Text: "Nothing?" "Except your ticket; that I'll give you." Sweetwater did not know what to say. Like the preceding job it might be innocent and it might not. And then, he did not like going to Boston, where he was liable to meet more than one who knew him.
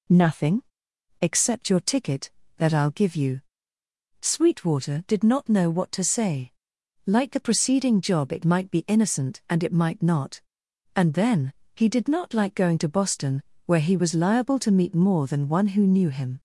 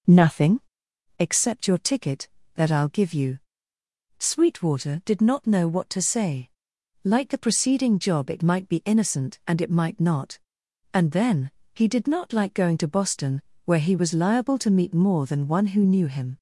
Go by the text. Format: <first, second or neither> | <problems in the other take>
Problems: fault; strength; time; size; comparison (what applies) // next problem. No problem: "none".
first | starts louder than the rest; noticeable; until 1.0 s; 4.5 dB